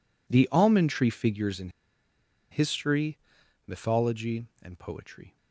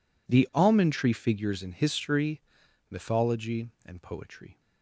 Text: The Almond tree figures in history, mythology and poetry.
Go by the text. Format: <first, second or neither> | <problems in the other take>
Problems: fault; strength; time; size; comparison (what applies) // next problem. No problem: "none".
second | pauses between "in" and "history"; noticeable; at 1.6 s; 0.82 s long